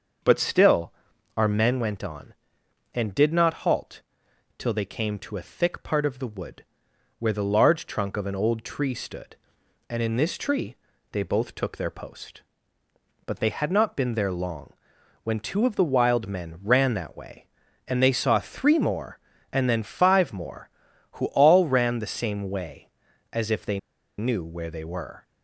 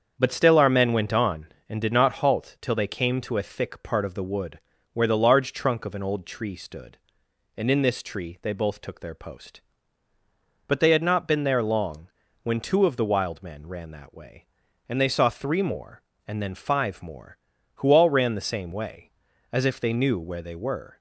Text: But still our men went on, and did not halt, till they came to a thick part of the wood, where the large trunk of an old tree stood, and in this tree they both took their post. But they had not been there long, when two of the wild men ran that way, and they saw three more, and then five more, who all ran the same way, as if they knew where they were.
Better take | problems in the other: second | starts louder than the rest; until 1.6 s; 6.5 dB; strong in the second // pauses between "still" and "our"; at 0.9 s; 0.44 s long // pauses between "tree" and "they"; slight; at 10.7 s; 0.36 s long // pauses between "they" and "knew"; at 23.7 s; 0.40 s long

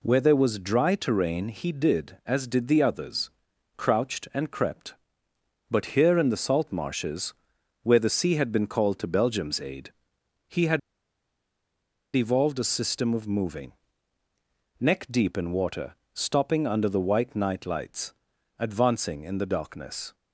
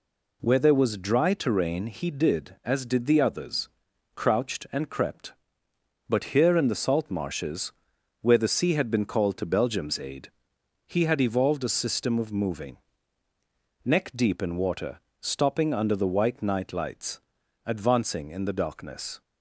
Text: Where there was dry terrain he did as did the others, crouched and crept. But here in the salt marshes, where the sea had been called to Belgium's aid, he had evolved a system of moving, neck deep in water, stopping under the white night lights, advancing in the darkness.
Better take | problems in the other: second | pauses between "had" and "evolved"; strong; at 10.7 s; 1.3 s long

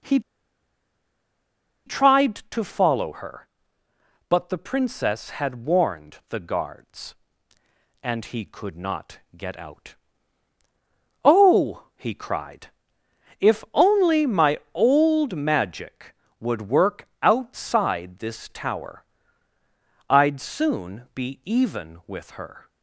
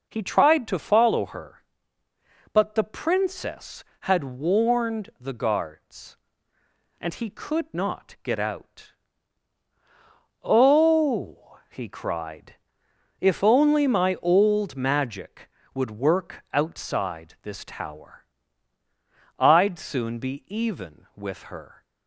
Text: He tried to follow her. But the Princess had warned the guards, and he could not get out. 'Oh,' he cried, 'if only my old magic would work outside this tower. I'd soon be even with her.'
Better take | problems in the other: second | pauses between "He" and "tried"; strong; at 0.1 s; 1.6 s long // pauses between "not" and "get"; slight; at 9.1 s; 0.16 s long

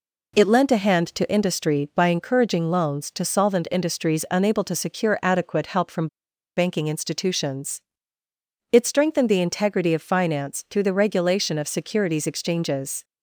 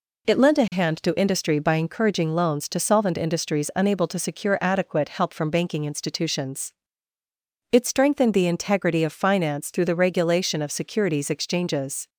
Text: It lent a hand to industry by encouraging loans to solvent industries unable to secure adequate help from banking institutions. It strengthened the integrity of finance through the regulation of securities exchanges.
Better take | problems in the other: second | pauses between "from" and "banking"; noticeable; at 6.0 s; 0.48 s long

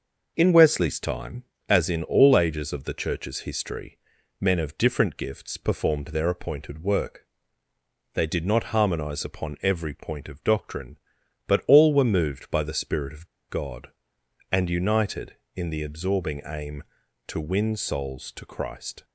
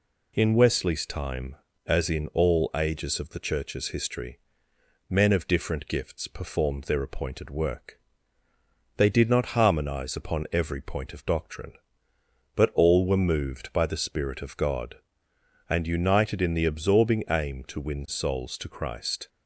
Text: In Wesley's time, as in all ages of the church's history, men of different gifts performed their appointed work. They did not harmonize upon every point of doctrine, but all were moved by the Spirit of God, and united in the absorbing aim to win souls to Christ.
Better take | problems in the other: second | pauses between "of" and "God"; slight; at 13.2 s; 0.21 s long

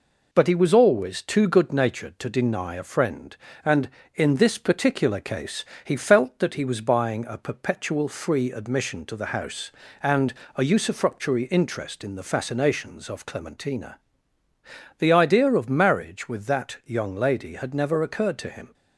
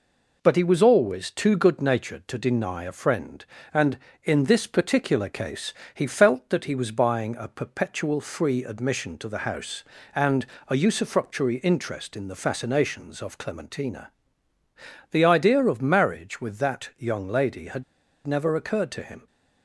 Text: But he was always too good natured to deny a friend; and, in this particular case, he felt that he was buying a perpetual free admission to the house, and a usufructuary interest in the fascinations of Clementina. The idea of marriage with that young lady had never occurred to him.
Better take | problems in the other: first | pauses between "and" and "a"; slight; at 10.4 s; 0.22 s long; slight in the first // pauses between "had" and "never"; at 17.8 s; 0.42 s long

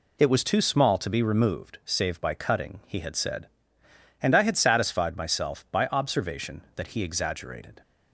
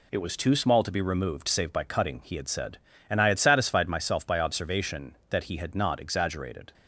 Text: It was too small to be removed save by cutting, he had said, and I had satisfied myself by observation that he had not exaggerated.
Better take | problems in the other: second | skips "had not"; at 7.0 s

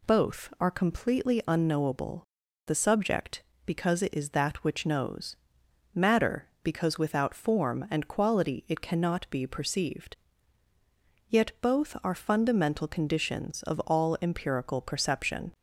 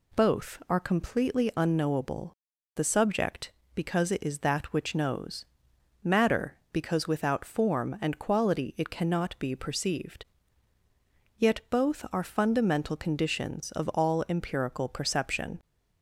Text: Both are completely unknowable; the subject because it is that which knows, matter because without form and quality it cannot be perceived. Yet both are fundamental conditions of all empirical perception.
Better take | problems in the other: neither | none

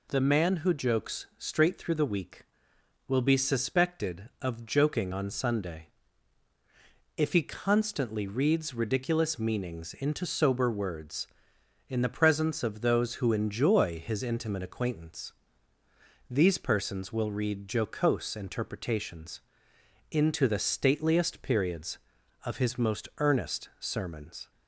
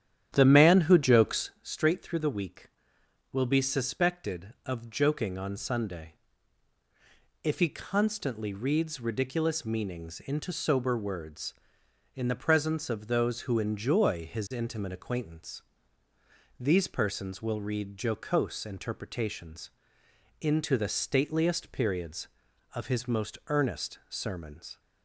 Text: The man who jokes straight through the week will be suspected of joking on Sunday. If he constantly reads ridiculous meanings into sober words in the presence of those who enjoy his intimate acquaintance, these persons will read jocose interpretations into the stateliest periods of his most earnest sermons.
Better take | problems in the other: first | starts louder than the rest; strong; until 1.6 s; 11 dB // pauses between "interpretations" and "into"; noticeable; at 19.6 s; 0.72 s long; noticeable in the first

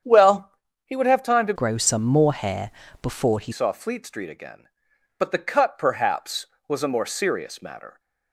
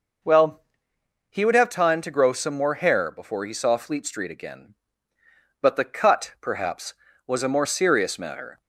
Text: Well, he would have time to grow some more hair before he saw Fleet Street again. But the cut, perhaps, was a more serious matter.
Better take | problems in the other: second | starts louder than the rest; strong; until 1.3 s; 8.5 dB // changes voice from "grow" to "he"; from 1.5 to 3.5 s; 2.0 s long // pauses between "hair" and "before"; slight; at 2.7 s; 0.32 s long

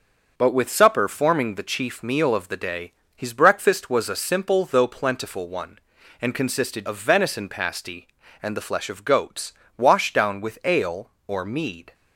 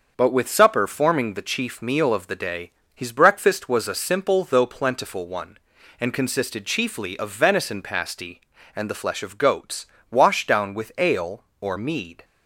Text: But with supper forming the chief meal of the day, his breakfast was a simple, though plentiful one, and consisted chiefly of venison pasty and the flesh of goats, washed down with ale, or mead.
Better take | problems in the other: second | starts louder than the rest; noticeable; until 1.3 s; 6 dB; also in the second // skips "chiefly"; at 6.8 s

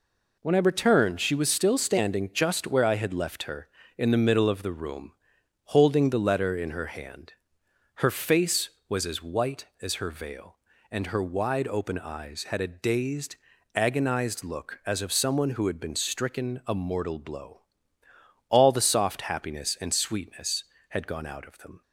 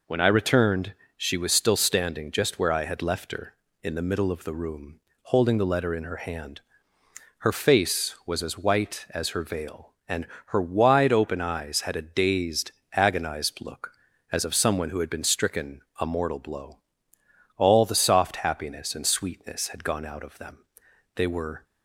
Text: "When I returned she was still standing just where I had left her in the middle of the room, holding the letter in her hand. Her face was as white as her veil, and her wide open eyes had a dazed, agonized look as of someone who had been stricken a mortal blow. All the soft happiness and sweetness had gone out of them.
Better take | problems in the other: first | pauses between "returned" and "she"; slight; at 0.9 s; 0.22 s long // pauses between "and" and "her"; slight; at 10.2 s; 0.22 s long // pauses between "stricken" and "a"; slight; at 15.8 s; 0.18 s long // goes on to say "They were"; slight; from 21.1 s on; 0.48 s long

